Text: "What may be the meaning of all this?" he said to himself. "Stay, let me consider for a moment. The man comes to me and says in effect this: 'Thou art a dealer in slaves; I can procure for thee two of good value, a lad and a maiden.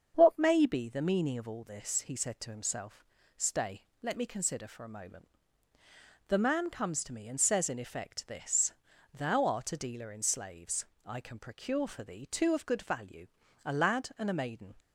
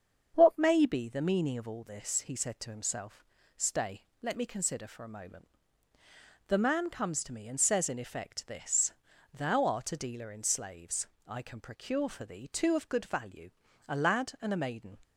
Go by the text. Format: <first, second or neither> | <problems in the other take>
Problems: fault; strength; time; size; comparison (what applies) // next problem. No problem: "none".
neither | starts louder than the rest; strong; the same in both